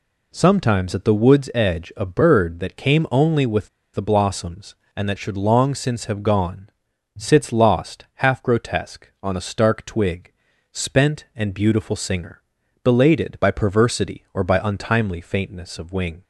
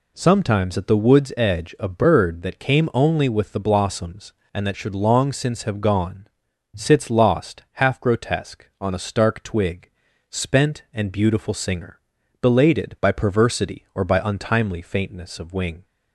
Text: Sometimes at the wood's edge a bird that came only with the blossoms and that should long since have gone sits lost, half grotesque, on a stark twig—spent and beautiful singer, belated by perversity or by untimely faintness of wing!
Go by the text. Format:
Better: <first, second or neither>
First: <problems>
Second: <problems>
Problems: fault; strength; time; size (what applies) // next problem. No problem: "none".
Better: second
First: pauses between "with" and "the"; slight; at 3.6 s; 0.25 s long // pauses between "gone" and "sits"; noticeable; at 6.6 s; 0.48 s long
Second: pauses between "gone" and "sits"; noticeable; at 6.2 s; 0.48 s long